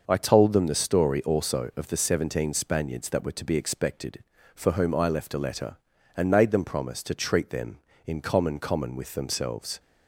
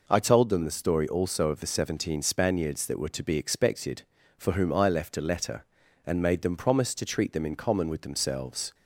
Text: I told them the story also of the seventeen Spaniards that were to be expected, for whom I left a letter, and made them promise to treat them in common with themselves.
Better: second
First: says "common" twice; at 8.5 s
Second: none

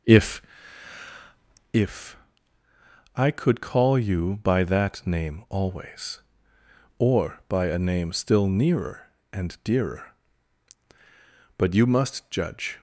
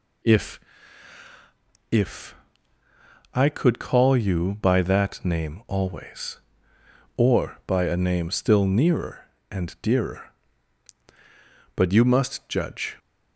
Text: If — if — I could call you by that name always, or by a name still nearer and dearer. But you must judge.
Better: second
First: starts louder than the rest; noticeable; until 1.8 s; 5 dB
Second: none

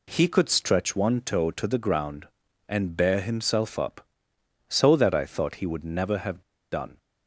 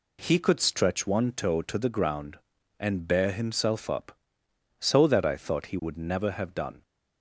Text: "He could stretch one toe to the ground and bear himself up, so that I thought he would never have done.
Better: second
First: pauses between "have" and "done"; slight; at 6.4 s; 0.31 s long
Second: none

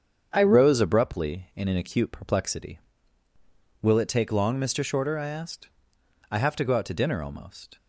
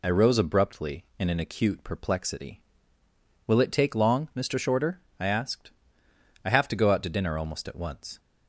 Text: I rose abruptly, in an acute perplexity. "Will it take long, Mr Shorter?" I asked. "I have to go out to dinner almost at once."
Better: second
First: starts louder than the rest; strong; until 1.3 s; 7.5 dB // stops before "at once"; at 7.7 s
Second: none

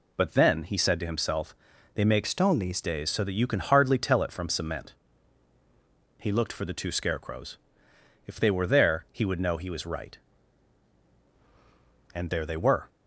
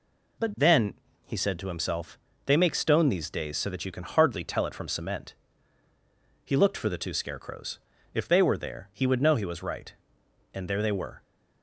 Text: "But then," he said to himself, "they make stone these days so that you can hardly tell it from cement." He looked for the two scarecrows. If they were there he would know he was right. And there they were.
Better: second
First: changes voice from "stone" to "these"; from 2.2 to 2.8 s; 0.6 s long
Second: none

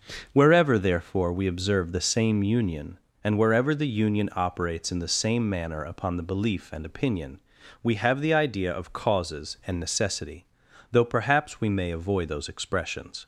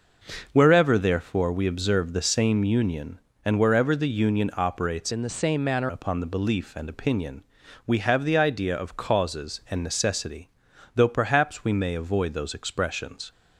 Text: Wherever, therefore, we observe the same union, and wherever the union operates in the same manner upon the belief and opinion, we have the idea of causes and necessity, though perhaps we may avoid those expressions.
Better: first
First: starts louder than the rest; until 1.3 s; 6.5 dB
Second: starts louder than the rest; noticeable; until 1.5 s; 6 dB // changes voice from "in" to "manner"; from 5.1 to 5.8 s; 0.7 s long

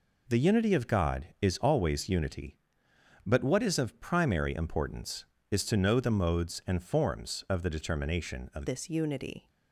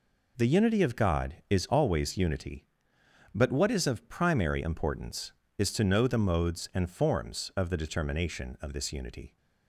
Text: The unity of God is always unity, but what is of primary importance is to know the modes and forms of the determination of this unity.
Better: second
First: changes voice at "this"; from 8.6 s on; 0.8 s long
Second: none

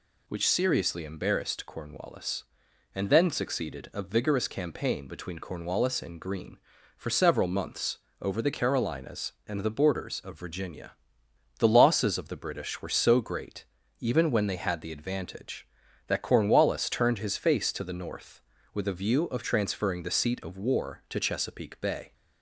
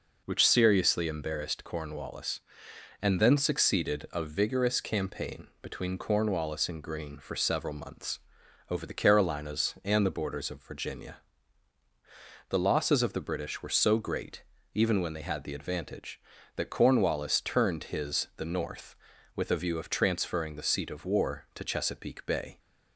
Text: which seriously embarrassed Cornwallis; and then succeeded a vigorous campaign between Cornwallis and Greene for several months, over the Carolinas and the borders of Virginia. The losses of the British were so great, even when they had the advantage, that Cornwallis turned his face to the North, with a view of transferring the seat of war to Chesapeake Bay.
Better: first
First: none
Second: skips "face to"; at 18.3 s

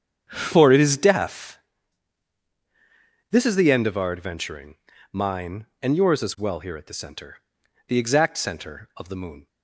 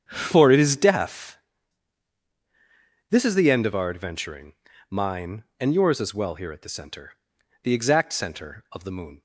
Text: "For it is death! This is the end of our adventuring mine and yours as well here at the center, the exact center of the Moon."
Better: neither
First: starts louder than the rest; strong; until 1.2 s; 8 dB // pauses between "adventuring" and "mine"; slight; at 4.7 s; 0.36 s long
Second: starts louder than the rest; strong; until 1.0 s; 8 dB // pauses between "adventuring" and "mine"; slight; at 4.5 s; 0.36 s long

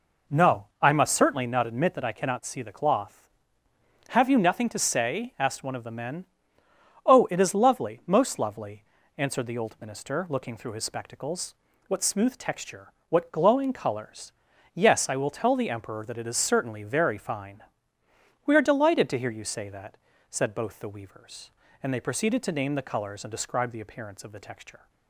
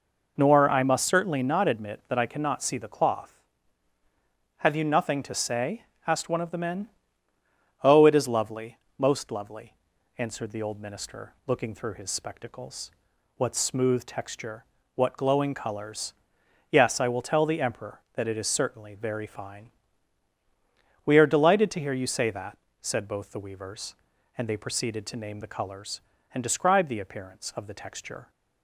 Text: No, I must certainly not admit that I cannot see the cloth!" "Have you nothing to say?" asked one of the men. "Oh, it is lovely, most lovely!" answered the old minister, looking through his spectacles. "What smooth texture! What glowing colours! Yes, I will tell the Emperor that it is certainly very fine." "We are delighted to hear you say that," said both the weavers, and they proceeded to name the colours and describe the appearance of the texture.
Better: first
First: none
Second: says "Nor" for "No"; at 0.3 s

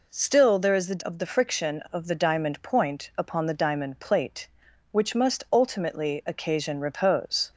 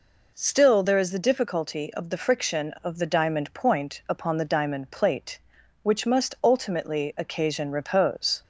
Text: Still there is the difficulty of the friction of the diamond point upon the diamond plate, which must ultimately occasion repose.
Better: second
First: skips "difficulty"; at 1.0 s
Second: none

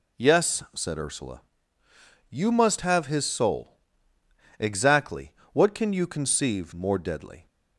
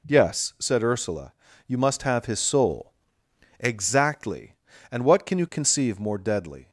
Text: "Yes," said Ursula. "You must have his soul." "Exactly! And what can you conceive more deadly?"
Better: second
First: skips "And"; at 5.4 s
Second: none

